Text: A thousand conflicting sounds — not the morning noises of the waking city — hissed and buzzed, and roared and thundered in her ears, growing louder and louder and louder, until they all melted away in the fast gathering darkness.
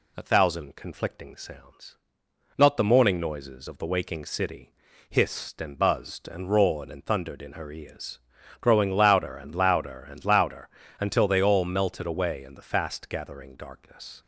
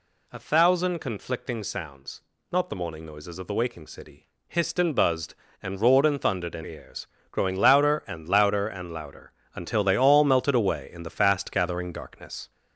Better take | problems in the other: first | skips "her"; at 6.6 s

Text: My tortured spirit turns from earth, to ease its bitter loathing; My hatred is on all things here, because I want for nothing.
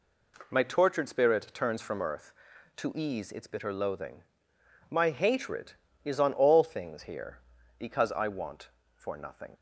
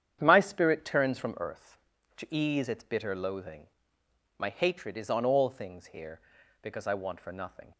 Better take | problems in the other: first | starts louder than the rest; strong; until 1.2 s; 9 dB // skips "tortured"; at 0.4 s

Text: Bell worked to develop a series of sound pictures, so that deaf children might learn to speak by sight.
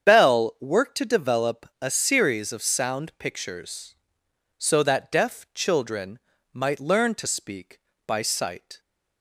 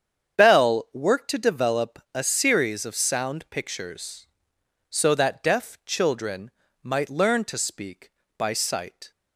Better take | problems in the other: neither | starts louder than the rest; strong; the same in both // pauses between "develop" and "a"; slight; the same in both // pauses between "children" and "might"; slight; the same in both

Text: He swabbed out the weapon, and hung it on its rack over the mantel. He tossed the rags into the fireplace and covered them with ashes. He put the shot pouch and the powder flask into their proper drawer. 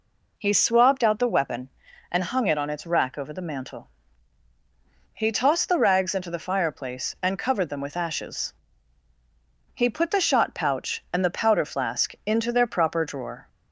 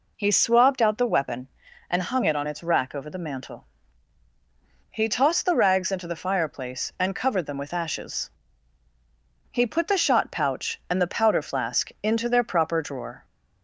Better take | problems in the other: neither | none

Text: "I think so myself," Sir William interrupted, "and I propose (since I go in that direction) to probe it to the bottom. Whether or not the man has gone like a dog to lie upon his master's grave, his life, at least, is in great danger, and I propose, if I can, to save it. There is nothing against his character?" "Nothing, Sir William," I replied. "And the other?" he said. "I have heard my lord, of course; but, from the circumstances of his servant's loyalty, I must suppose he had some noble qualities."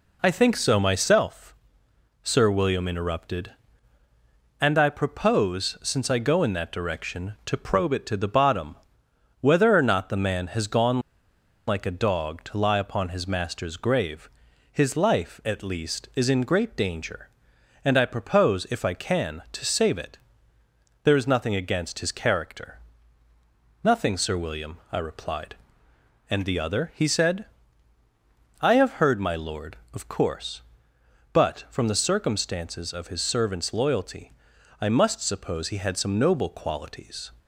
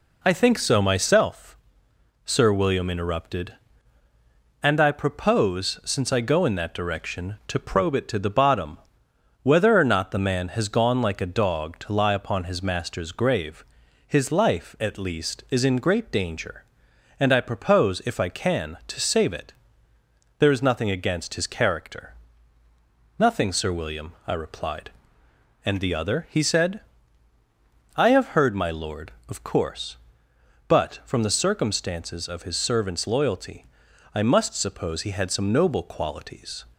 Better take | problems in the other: second | pauses between "gone" and "like"; noticeable; at 10.9 s; 0.68 s long

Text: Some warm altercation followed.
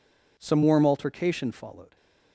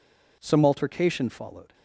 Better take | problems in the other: first | skips "warm"; at 0.6 s

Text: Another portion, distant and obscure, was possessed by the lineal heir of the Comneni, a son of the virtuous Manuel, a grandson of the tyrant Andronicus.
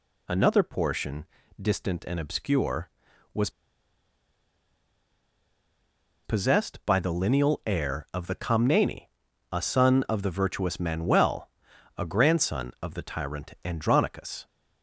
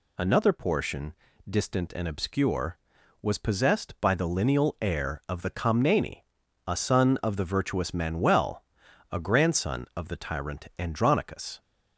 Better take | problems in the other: second | pauses between "was" and "possessed"; strong; at 3.4 s; 2.7 s long

